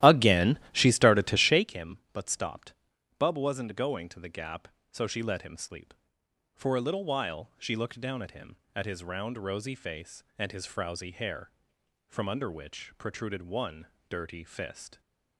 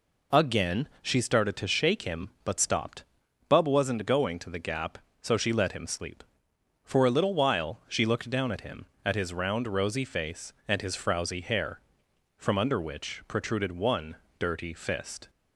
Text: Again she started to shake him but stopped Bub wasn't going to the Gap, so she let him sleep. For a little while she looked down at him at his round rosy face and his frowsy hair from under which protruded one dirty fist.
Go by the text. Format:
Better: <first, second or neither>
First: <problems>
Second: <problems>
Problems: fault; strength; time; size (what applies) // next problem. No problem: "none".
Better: second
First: starts louder than the rest; strong; until 1.7 s; 14 dB // pauses between "stopped" and "Bub"; noticeable; at 2.7 s; 0.46 s long // pauses between "one" and "dirty"; slight; at 13.8 s; 0.22 s long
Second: pauses between "stopped" and "Bub"; noticeable; at 3.0 s; 0.46 s long // pauses between "one" and "dirty"; slight; at 14.1 s; 0.22 s long